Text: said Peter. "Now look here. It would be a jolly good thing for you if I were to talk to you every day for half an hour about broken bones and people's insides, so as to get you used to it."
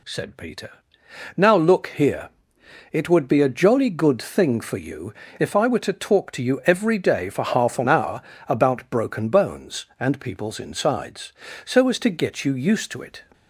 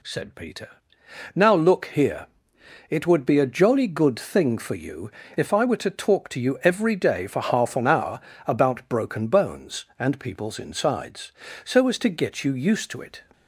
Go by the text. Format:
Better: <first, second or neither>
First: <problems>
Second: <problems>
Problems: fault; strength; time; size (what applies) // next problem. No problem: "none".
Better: neither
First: pauses between "you" and "if"; slight; at 5.1 s; 0.26 s long // pauses between "hour" and "about"; slight; at 8.2 s; 0.28 s long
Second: pauses between "you" and "if"; slight; at 5.0 s; 0.26 s long // pauses between "hour" and "about"; slight; at 8.1 s; 0.28 s long